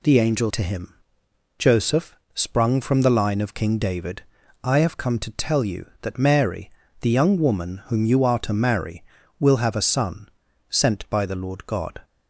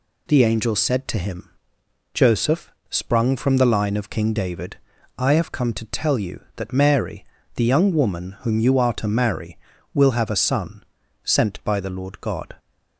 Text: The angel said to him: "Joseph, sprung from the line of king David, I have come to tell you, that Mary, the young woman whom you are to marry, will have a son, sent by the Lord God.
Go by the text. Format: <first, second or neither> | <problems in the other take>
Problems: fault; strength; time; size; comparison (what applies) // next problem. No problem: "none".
second | skips "said"; at 0.5 s